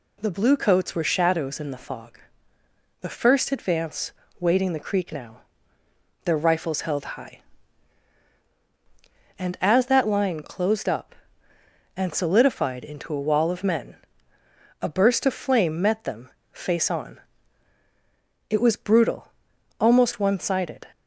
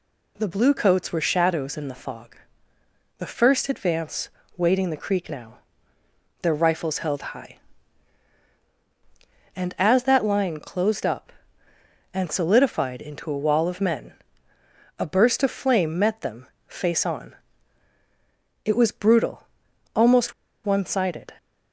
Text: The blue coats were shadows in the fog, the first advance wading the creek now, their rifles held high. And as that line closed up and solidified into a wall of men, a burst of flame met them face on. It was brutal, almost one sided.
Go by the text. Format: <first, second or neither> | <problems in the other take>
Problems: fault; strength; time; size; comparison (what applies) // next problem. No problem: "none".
first | pauses between "advance" and "wading"; slight; at 4.3 s; 0.26 s long; slight in the first // pauses between "them" and "face"; slight; at 16.4 s; 0.18 s long; slight in the first // pauses between "almost" and "one"; slight; at 20.3 s; 0.32 s long